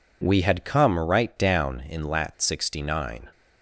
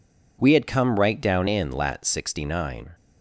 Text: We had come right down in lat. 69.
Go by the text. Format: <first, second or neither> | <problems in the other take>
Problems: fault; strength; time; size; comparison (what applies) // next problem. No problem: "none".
neither | none